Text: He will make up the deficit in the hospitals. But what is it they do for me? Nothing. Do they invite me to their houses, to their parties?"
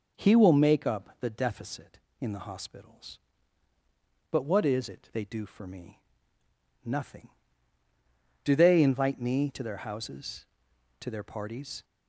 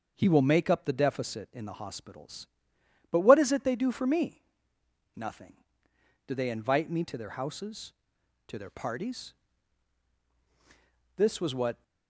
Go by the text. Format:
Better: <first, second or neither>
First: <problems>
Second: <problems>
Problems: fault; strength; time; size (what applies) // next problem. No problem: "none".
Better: first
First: none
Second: starts louder than the rest; until 1.1 s; 6 dB // goes on to say "This was what"; noticeable; from 11.1 s on; 0.66 s long